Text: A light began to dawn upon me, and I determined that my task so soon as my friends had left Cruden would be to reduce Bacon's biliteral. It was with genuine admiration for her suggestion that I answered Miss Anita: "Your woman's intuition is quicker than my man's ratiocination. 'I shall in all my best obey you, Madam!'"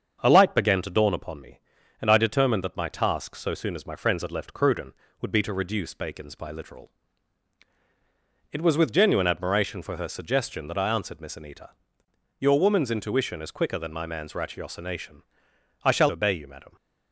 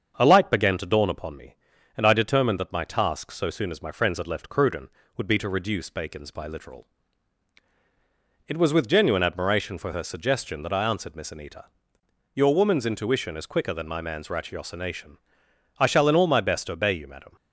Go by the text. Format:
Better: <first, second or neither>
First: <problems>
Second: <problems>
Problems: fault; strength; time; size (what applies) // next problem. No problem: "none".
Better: second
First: starts louder than the rest; until 1.2 s; 7 dB // skips "in all my best"; at 16.0 s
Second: starts louder than the rest; until 1.1 s; 7 dB